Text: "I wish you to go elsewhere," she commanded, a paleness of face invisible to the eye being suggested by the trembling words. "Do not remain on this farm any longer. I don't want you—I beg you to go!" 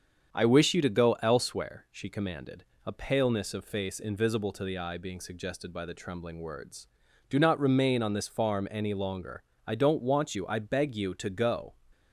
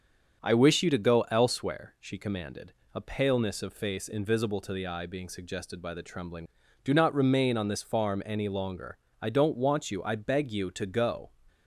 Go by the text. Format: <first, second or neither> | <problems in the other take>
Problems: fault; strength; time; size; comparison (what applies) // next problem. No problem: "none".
first | starts louder than the rest; strong; until 1.4 s; 7 dB; strong in the first // skips "words"; at 6.6 s